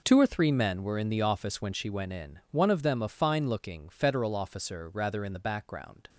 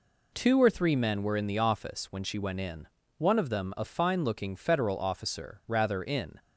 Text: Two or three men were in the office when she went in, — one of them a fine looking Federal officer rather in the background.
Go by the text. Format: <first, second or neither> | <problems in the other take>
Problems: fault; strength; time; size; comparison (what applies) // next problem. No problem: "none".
first | stops before "the background"; at 6.3 s